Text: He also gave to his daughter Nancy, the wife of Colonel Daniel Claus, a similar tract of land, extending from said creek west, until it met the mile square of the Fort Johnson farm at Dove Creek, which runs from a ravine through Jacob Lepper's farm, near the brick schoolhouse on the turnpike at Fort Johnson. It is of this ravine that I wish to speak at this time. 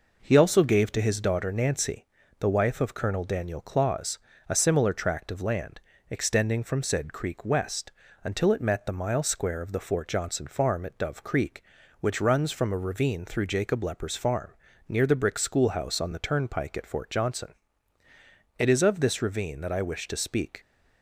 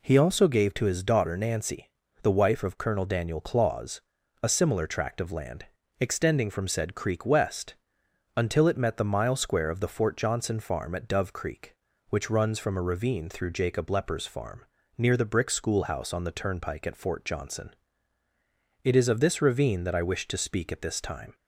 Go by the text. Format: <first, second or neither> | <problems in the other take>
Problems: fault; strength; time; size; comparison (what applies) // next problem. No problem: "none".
second | stops before "at this time"; at 20.5 s